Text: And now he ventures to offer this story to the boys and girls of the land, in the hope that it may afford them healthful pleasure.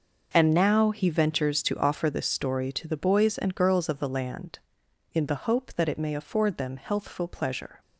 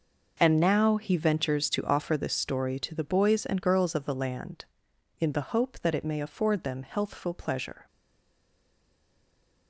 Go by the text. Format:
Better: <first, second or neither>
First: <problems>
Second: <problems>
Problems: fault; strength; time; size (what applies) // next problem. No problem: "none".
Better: first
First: none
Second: stays silent after the last word; noticeable; from 7.8 s on; 1.8 s long